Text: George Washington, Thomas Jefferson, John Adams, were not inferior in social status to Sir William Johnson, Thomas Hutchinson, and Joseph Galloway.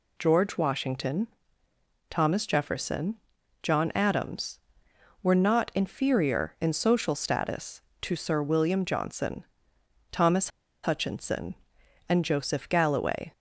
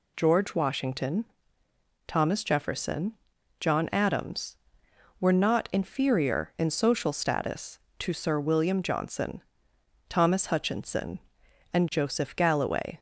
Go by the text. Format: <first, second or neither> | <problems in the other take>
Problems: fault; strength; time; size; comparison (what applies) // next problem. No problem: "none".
second | pauses between "Thomas" and "Hutchinson"; slight; at 10.4 s; 0.34 s long